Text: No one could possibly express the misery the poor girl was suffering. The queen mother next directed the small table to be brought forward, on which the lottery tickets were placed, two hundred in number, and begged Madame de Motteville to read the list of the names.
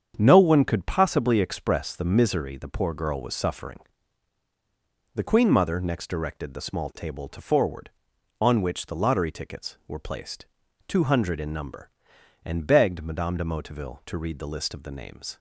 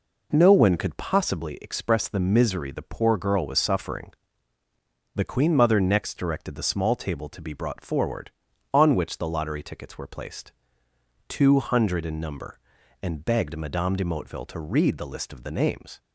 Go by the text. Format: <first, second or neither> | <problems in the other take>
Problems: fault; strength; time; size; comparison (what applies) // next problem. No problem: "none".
second | starts louder than the rest; strong; until 1.1 s; 8 dB // skips "be brought"; at 7.4 s